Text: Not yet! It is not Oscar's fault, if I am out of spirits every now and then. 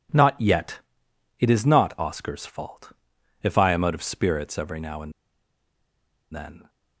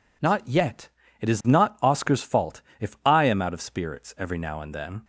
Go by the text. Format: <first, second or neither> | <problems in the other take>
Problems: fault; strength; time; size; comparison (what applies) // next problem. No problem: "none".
second | pauses between "and" and "then"; at 5.1 s; 1.2 s long